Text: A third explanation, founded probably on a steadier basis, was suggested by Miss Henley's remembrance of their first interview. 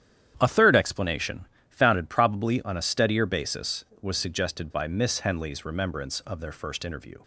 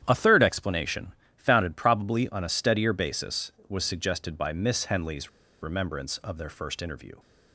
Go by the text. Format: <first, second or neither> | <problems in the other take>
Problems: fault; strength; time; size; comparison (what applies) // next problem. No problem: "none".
first | starts louder than the rest; strong; until 1.0 s; 10 dB; strong in the first // pauses between "Henley's" and "remembrance"; slight; at 5.2 s; 0.32 s long